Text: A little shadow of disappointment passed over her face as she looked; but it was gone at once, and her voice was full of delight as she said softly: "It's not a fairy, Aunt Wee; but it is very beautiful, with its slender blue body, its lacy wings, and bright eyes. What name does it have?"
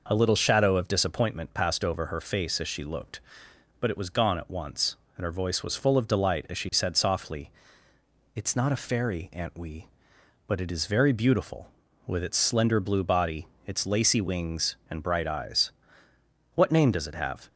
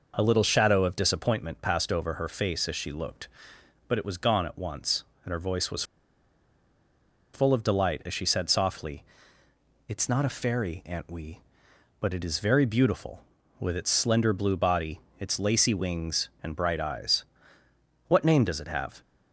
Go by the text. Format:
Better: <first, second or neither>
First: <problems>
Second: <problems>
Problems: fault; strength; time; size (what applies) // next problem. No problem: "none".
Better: first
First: none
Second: pauses between "was" and "full"; strong; at 5.8 s; 1.5 s long